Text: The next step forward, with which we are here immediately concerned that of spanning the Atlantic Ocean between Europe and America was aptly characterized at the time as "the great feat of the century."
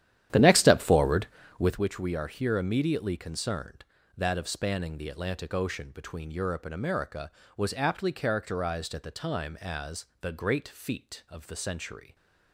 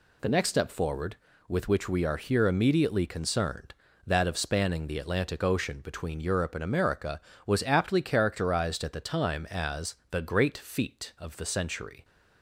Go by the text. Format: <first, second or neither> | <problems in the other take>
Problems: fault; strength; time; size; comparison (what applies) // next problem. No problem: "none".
second | starts louder than the rest; strong; until 1.8 s; 11 dB // pauses between "as" and "the"; slight; at 10.0 s; 0.16 s long; slight in the second